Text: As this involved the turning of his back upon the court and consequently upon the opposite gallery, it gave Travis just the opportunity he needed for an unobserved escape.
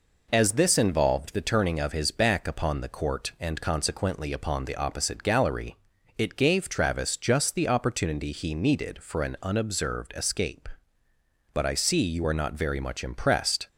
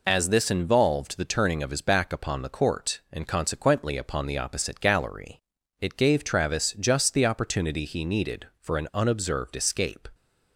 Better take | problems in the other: second | goes on to say "But I see you are not very much impressed"; strong; from 11.5 s on; 2.1 s long

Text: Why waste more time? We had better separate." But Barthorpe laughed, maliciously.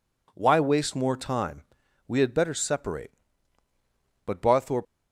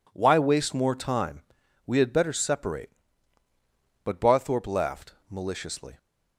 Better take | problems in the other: second | stops before "laughed maliciously"; at 4.8 s

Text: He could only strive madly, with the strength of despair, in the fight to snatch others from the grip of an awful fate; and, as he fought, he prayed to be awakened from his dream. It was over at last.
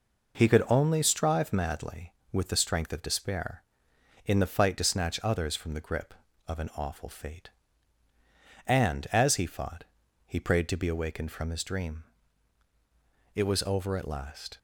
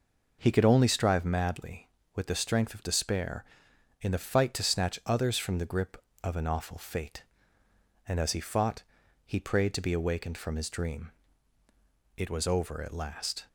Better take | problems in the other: neither | none

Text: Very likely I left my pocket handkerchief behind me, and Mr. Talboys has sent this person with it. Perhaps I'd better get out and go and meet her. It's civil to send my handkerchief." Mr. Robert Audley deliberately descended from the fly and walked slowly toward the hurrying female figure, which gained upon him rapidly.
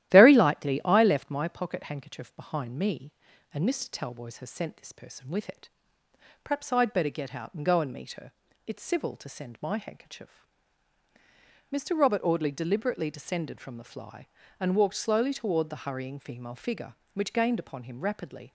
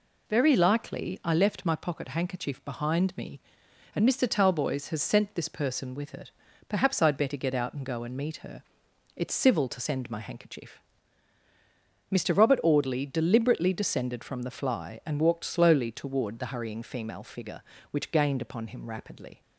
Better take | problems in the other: second | starts louder than the rest; strong; until 1.3 s; 13.5 dB

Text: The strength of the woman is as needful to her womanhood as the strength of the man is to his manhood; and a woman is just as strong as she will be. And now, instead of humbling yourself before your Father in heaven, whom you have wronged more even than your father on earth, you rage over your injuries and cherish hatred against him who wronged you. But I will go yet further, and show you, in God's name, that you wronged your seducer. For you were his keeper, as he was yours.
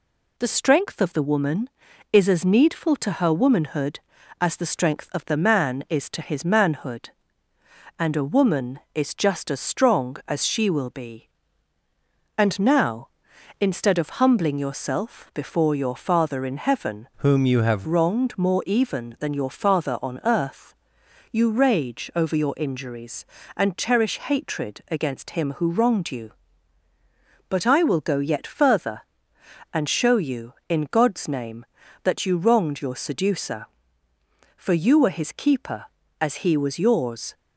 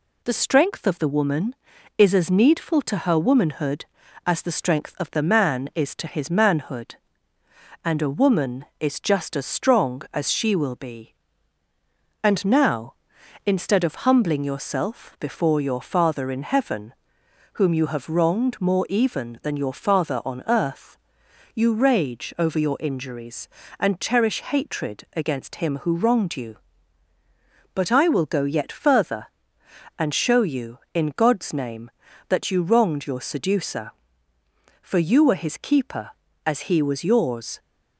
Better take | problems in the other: second | changes voice from "whom" to "have"; from 17.1 to 17.8 s; 0.7 s long

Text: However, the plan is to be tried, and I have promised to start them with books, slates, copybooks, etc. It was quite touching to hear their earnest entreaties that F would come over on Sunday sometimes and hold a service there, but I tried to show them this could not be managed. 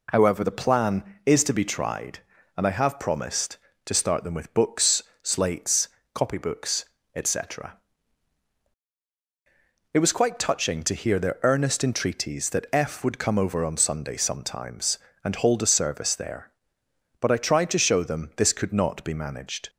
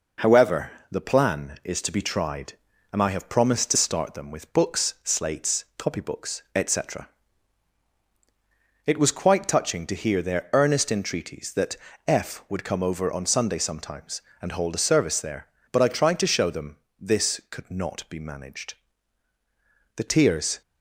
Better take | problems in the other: first | pauses between "that" and "F"; slight; at 11.7 s; 0.30 s long // pauses between "them" and "this"; slight; at 16.7 s; 0.22 s long // goes on to say "The tears"; noticeable; from 19.9 s on; 0.64 s long

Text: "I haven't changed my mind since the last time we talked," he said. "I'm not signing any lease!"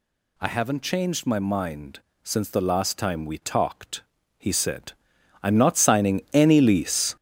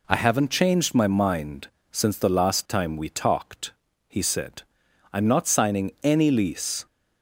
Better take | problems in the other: second | gets louder; strong; throughout; 8 dB // pauses between "mind" and "since"; slight; at 2.0 s; 0.22 s long; slight in the second

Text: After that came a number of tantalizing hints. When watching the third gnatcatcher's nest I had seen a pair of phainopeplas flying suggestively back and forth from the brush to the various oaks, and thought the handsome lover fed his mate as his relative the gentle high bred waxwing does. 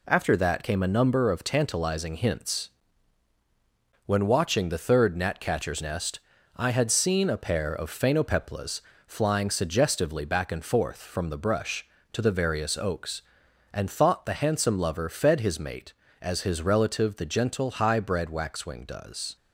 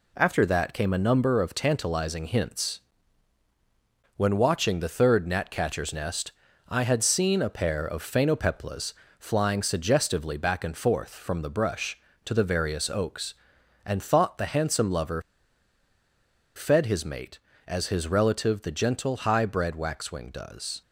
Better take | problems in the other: first | pauses between "nest" and "I"; slight; at 6.3 s; 0.36 s long; slight in the first // pauses between "phainopeplas" and "flying"; slight; at 8.9 s; 0.24 s long; slight in the first // pauses between "lover" and "fed"; strong; at 15.1 s; 1.3 s long

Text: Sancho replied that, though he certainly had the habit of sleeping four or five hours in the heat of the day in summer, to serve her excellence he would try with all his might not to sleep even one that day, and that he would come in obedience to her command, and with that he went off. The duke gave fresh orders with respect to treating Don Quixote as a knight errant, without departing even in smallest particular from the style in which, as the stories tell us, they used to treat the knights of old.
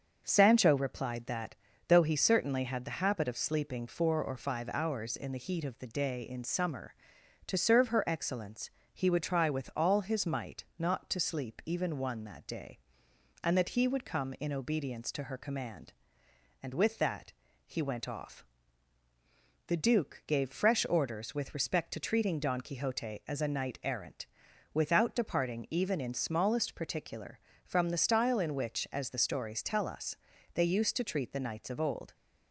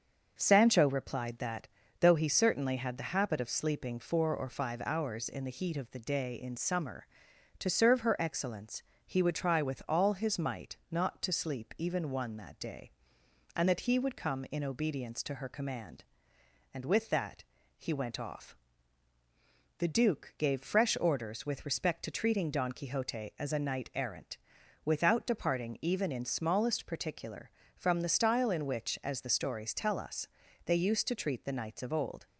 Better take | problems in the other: neither | pauses between "excellence" and "he"; slight; the same in both // pauses between "that" and "he"; slight; the same in both

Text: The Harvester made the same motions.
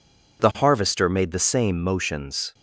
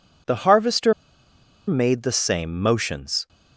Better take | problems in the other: first | pauses between "Harvester" and "made"; noticeable; at 0.9 s; 0.74 s long

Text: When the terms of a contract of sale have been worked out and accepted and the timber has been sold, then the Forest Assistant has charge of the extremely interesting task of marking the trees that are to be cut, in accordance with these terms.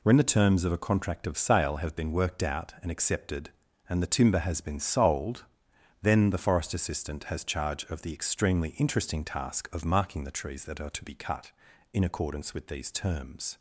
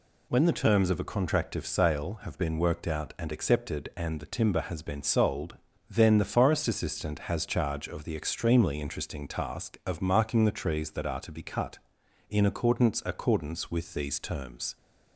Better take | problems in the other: first | says "accordance" twice; at 13.0 s

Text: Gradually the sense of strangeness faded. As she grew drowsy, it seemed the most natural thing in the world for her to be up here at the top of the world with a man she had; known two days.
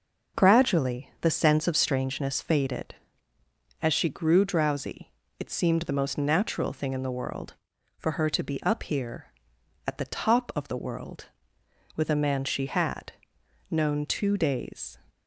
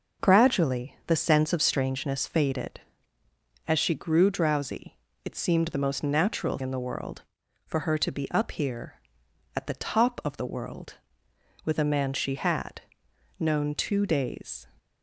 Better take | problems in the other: first | skips "thing"; at 6.5 s

